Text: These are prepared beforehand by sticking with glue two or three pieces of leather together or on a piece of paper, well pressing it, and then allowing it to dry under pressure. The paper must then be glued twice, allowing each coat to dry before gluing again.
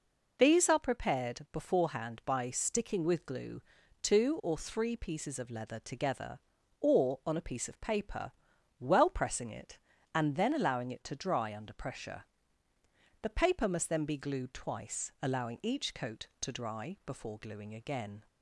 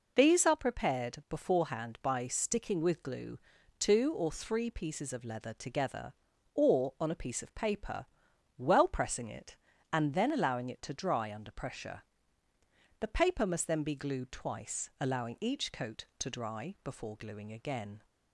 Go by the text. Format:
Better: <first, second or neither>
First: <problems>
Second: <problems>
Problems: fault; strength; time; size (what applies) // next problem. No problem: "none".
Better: neither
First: pauses between "glue" and "two"; at 3.6 s; 0.40 s long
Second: pauses between "glue" and "two"; at 3.3 s; 0.40 s long